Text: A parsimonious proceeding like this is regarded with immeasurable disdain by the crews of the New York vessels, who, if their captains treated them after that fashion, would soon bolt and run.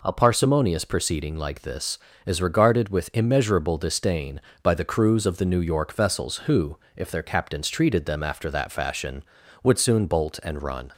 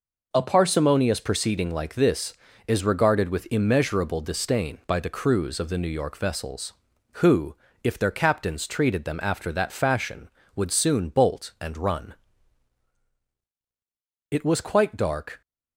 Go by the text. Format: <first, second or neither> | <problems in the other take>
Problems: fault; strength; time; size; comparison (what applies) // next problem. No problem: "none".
first | goes on to say "It was quite dark"; noticeable; from 14.2 s on; 1.1 s long